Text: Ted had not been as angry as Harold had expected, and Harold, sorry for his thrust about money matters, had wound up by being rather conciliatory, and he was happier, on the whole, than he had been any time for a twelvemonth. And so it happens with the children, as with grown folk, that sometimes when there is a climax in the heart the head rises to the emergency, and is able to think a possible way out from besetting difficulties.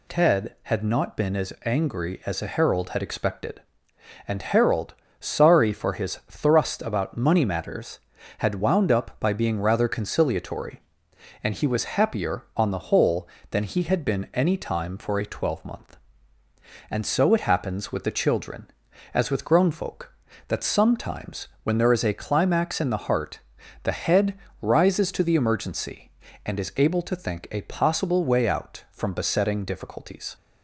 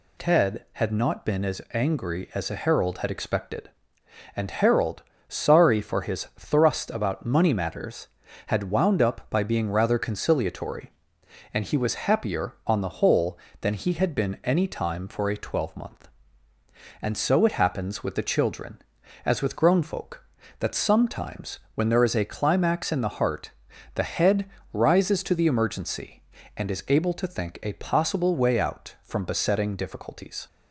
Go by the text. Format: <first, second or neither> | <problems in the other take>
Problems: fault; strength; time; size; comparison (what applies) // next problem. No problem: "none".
neither | pauses between "sometimes" and "when"; slight; the same in both // pauses between "heart" and "the"; the same in both // pauses between "head" and "rises"; slight; the same in both